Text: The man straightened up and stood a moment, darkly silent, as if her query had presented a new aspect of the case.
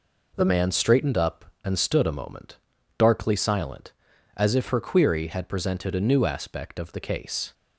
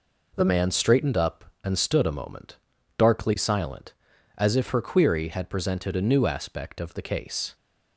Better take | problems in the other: neither | none

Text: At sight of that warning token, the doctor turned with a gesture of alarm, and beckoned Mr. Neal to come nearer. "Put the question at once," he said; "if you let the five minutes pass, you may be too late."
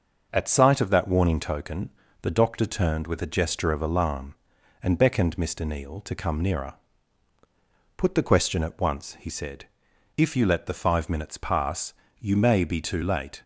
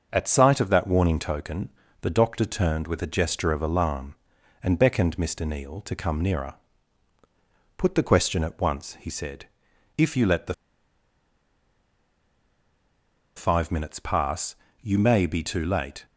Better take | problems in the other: first | pauses between "the" and "five"; strong; at 10.5 s; 2.8 s long

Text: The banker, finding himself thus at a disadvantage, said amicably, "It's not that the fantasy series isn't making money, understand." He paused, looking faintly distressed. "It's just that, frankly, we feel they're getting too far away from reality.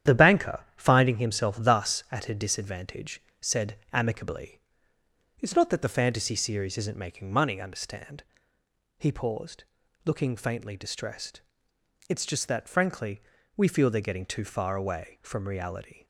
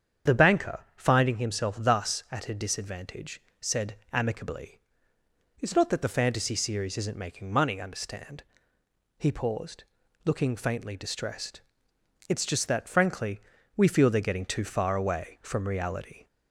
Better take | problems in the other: second | gets quieter; throughout; 6.5 dB // starts louder than the rest; strong; until 1.2 s; 10 dB; strong in the second // pauses between "said" and "amicably"; slight; at 3.7 s; 0.18 s long; slight in the second

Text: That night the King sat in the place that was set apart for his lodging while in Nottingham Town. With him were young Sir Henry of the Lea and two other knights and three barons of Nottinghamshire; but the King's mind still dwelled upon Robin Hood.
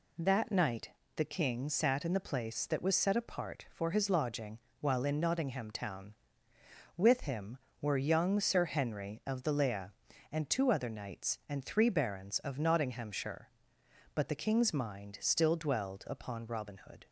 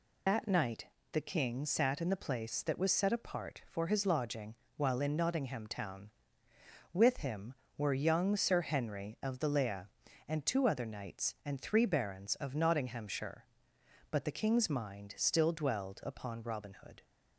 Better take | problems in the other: first | loses the start of "That"; at 0.2 s; 130 ms // pauses between "night" and "the"; slight; at 0.8 s; 0.26 s long; slight in the first // pauses between "lodging" and "while"; slight; at 4.5 s; 0.20 s long; slight in the first

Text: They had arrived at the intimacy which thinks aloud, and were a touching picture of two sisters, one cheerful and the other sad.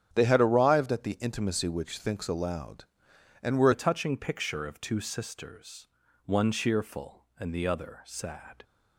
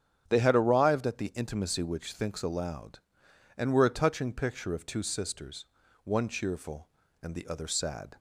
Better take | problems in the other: second | starts louder than the rest; strong; until 1.1 s; 9.5 dB; strong in the second // changes voice at "a"; from 3.7 s on; 4.9 s long

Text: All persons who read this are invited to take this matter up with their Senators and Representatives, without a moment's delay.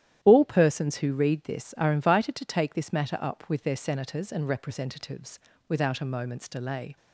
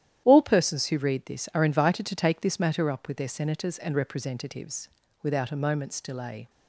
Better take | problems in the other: neither | starts louder than the rest; strong; the same in both

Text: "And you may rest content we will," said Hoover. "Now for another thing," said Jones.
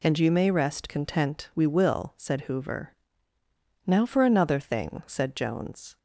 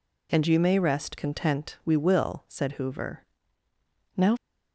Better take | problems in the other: first | stops before "for another thing said Jones"; at 4.3 s

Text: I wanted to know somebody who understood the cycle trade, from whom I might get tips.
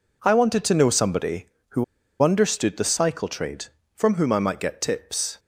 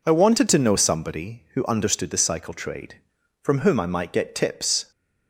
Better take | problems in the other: second | pauses between "who" and "understood"; at 1.8 s; 0.38 s long

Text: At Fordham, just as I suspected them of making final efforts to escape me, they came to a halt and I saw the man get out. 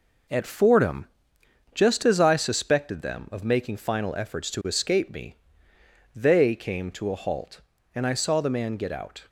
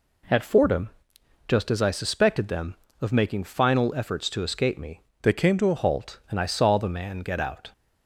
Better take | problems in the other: first | changes voice from "they" to "a"; from 5.2 to 5.7 s; 0.5 s long

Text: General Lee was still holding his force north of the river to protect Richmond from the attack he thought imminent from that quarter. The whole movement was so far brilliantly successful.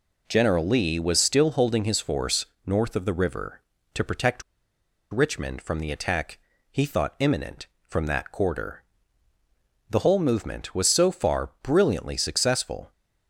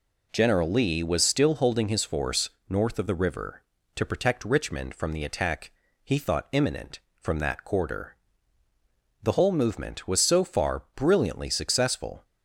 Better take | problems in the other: second | pauses between "force" and "north"; slight; at 2.4 s; 0.20 s long; slight in the second // pauses between "protect" and "Richmond"; noticeable; at 4.4 s; 0.69 s long // pauses between "attack" and "he"; slight; at 6.3 s; 0.34 s long; slight in the second

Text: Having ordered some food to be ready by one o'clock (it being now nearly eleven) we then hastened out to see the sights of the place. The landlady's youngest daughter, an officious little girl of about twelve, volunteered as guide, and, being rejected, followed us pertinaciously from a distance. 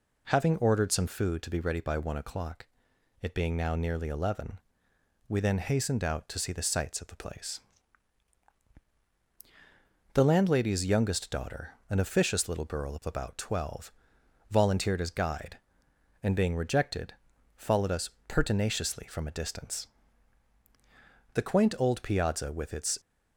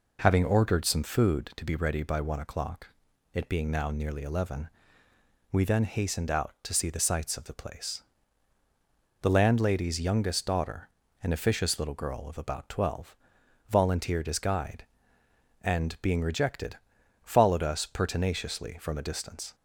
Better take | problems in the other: second | pauses between "us" and "pertinaciously"; slight; at 18.1 s; 0.16 s long // goes on to say "The quaint old piazza with its"; from 21.3 s on; 1.6 s long

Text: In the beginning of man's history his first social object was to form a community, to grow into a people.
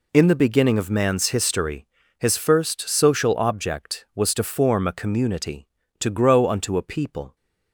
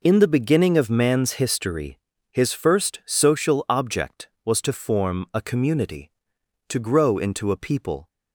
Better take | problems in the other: second | pauses between "history" and "his"; slight; at 1.8 s; 0.32 s long; slight in the second // says "unto" for "into"; at 6.4 s

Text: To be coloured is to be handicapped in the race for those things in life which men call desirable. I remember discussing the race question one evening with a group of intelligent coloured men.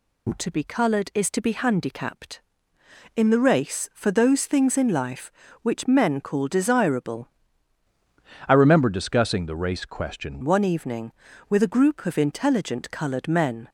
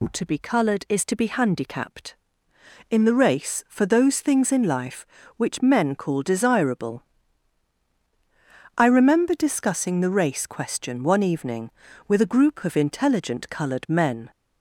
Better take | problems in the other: second | changes voice from "I" to "question"; from 8.4 to 10.4 s; 2.0 s long

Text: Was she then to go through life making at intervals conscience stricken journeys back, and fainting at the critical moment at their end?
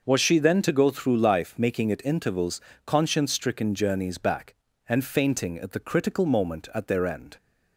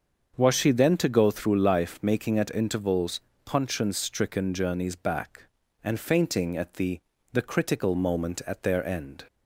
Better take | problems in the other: first | starts louder than the rest; until 1.3 s; 7 dB // pauses between "intervals" and "conscience"; slight; at 3.2 s; 0.26 s long; slight in the first // says "the" twice; at 7.3 s

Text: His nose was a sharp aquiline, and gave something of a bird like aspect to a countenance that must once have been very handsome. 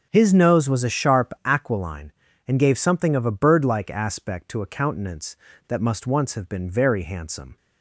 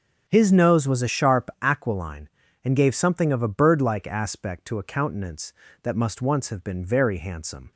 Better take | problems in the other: neither | starts louder than the rest; strong; the same in both

